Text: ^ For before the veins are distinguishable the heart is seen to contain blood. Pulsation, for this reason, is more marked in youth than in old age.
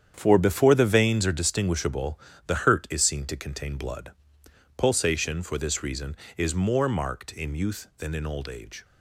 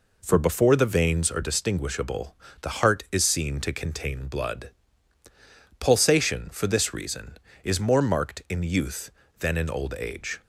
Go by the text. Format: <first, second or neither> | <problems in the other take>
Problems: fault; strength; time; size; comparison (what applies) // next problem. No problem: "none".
second | starts louder than the rest; strong; until 1.1 s; 8.5 dB // pauses between "distinguishable" and "the"; slight; at 2.1 s; 0.26 s long; slight in the second // says "hurt" for "heart"; at 2.6 s